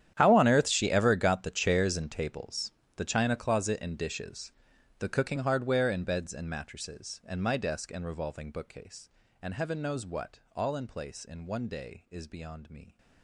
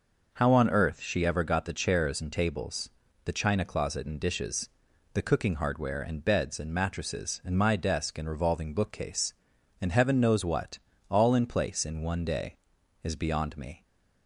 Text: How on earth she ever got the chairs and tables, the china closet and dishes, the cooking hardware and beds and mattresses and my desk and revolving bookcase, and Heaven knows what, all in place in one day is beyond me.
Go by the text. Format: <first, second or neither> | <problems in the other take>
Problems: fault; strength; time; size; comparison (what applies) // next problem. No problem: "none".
second | gets quieter; strong; throughout; 19 dB